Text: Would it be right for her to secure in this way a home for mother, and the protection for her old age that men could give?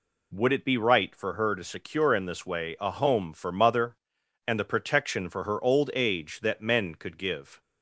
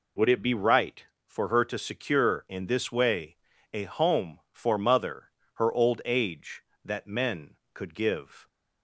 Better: first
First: none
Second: pauses between "way" and "a"; slight; at 3.3 s; 0.36 s long // skips "and the protection for"; at 5.4 s

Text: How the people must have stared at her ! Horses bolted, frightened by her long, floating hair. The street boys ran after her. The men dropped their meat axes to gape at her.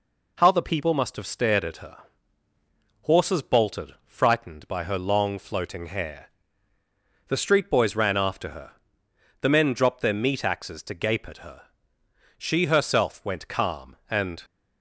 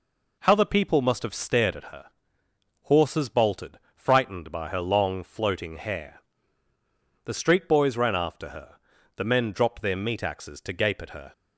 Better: second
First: goes on to say "She herself went calm and"; strong; from 12.3 s on; 2.0 s long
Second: none

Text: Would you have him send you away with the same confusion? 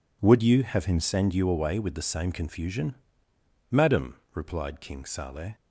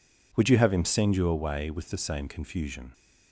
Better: second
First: goes on to say "Madam replied King Saleh"; strong; from 3.7 s on; 1.8 s long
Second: none

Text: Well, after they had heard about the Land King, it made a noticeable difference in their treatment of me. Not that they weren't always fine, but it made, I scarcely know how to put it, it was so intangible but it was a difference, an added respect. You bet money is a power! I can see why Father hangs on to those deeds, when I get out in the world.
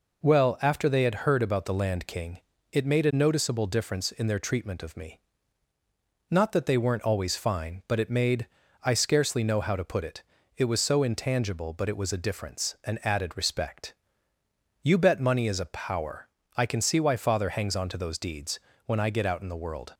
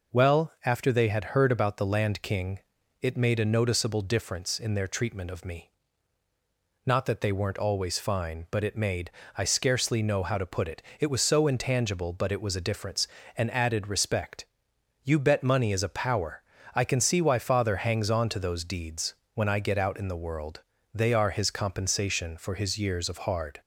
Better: first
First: none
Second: goes on to say "They are his compensation for his years of hard"; strong; from 20.9 s on; 2.6 s long

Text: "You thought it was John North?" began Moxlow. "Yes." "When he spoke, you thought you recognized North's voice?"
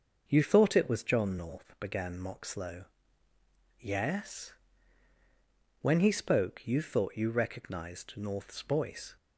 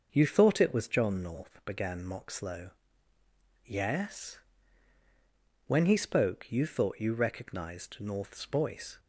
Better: neither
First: starts louder than the rest; until 1.2 s; 6.5 dB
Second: starts louder than the rest; until 1.1 s; 6.5 dB

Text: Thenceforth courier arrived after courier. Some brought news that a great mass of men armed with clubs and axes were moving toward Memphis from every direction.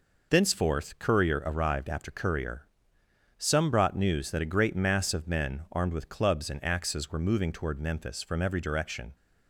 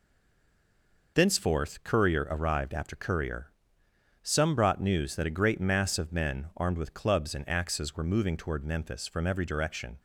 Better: first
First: none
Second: stays silent before the first word; until 1.1 s; 1.1 s long

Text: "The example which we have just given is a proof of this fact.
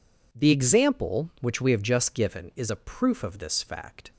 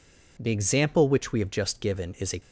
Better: first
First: none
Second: stops before "proof of this fact"; at 2.3 s

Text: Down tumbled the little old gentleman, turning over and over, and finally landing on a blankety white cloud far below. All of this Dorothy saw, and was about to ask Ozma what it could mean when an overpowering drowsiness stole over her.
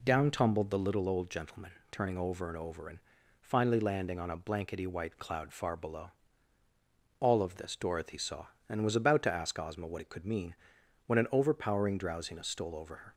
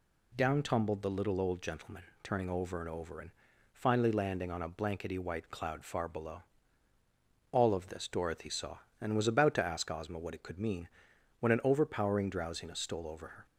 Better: second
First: starts louder than the rest; slight; until 1.0 s; 3 dB // pauses between "and" and "finally"; at 2.9 s; 0.42 s long // pauses between "mean" and "when"; noticeable; at 10.5 s; 0.52 s long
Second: pauses between "and" and "finally"; at 3.2 s; 0.42 s long // pauses between "mean" and "when"; noticeable; at 10.8 s; 0.52 s long

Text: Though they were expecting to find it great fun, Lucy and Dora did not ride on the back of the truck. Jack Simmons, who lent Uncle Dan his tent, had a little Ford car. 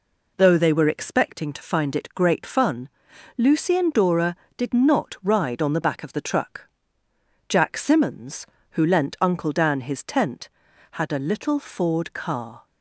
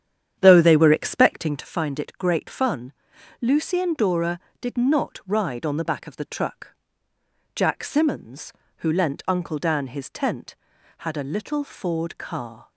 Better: first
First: none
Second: starts louder than the rest; strong; until 1.8 s; 9 dB

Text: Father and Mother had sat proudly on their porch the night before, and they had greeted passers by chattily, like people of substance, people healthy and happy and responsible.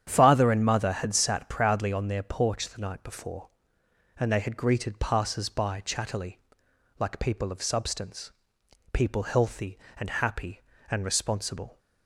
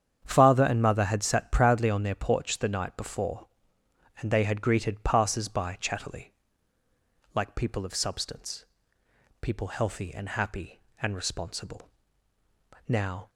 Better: first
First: starts louder than the rest; strong; until 1.0 s; 9.5 dB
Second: starts louder than the rest; strong; until 1.2 s; 8.5 dB // goes on to say "Now"; slight; from 12.8 s on; 0.42 s long

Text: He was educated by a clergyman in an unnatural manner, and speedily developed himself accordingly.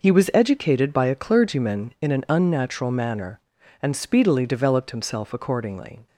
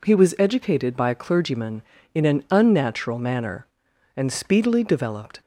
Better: first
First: none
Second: stops before "himself accordingly"; at 5.4 s

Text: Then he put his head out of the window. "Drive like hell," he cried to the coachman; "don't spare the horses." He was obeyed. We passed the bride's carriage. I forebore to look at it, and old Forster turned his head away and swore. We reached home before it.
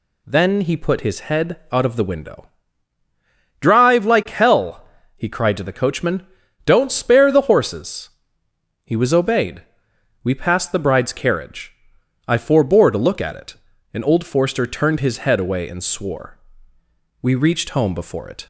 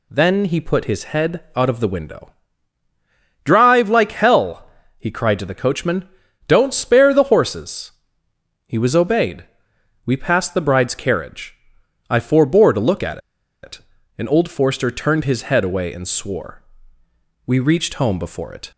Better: first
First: pauses between "head" and "out"; slight; at 1.5 s; 0.16 s long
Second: pauses between "head" and "out"; slight; at 1.4 s; 0.16 s long // pauses between "at" and "it"; at 13.1 s; 0.44 s long

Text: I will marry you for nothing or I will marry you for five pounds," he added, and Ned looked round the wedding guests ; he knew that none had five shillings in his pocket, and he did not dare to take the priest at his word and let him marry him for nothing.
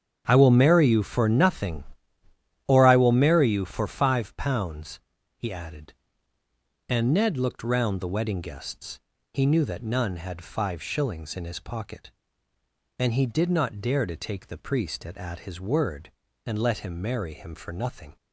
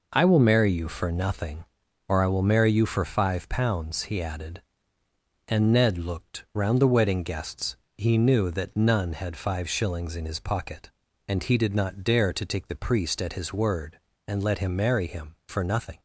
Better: second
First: starts louder than the rest; strong; until 1.2 s; 8.5 dB // says "at" twice; at 15.1 s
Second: none

